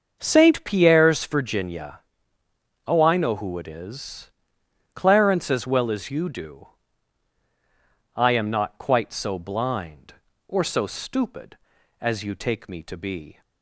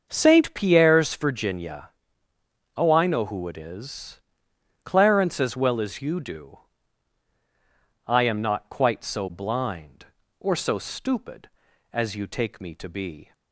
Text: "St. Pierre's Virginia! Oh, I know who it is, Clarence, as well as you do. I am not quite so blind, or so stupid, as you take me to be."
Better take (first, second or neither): neither